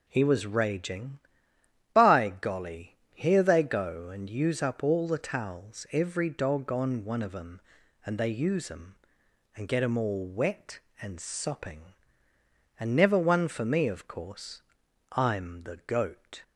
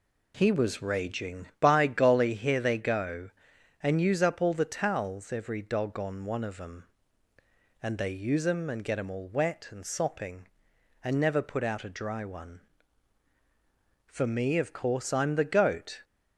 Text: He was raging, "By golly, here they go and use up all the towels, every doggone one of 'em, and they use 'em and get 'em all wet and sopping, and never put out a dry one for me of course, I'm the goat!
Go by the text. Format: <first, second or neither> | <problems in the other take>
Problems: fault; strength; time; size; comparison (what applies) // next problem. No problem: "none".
second | skips "put out a dry"; at 13.1 s